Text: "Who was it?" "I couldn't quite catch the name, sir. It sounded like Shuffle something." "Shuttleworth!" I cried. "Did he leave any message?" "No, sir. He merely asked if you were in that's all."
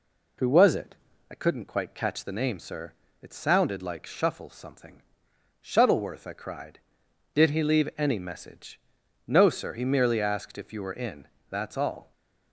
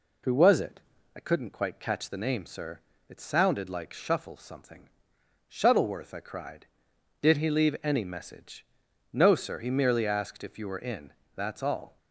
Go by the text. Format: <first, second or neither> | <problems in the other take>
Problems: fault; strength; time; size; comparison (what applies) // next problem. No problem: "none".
neither | pauses between "in" and "that's"; slight; the same in both